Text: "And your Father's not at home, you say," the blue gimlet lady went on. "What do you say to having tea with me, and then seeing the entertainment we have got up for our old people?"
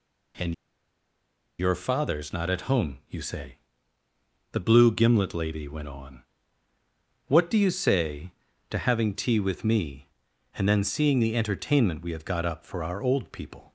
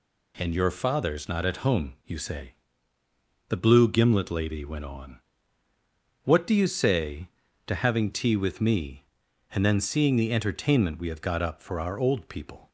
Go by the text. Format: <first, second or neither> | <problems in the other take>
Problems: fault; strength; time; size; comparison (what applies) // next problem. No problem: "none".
second | pauses between "And" and "your"; at 0.5 s; 1.0 s long